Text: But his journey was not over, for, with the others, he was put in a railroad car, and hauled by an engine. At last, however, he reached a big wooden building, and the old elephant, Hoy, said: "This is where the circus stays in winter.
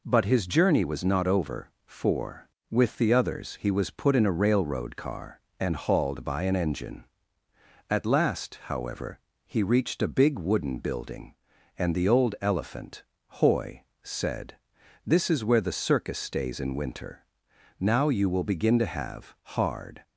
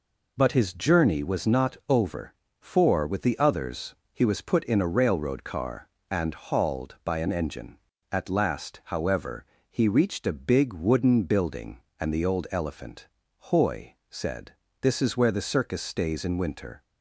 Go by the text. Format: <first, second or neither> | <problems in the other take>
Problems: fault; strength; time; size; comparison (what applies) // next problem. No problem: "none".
second | goes on to say "Now you will begin to have hard"; strong; from 17.7 s on; 2.2 s long